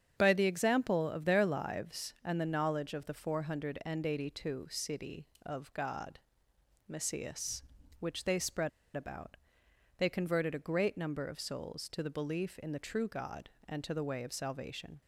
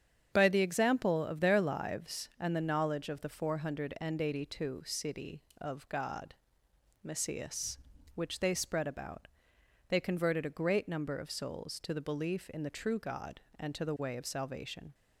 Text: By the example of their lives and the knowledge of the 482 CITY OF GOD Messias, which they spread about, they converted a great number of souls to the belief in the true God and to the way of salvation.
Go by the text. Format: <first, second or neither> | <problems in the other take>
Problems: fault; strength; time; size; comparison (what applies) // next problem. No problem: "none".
second | starts louder than the rest; strong; until 1.1 s; 8 dB; strong in the second // pauses between "GOD" and "Messias"; noticeable; at 6.2 s; 0.68 s long; noticeable in the second // pauses between "spread" and "about"; slight; at 8.6 s; 0.27 s long